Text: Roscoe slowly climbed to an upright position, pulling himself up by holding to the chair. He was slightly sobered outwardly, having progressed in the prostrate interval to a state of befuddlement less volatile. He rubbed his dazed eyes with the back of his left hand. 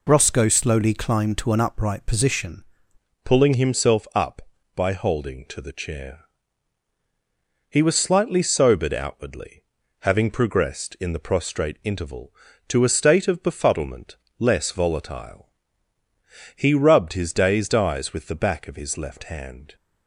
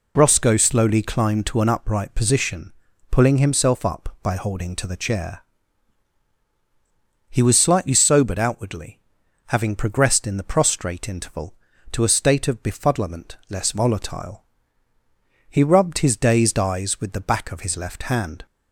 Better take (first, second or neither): second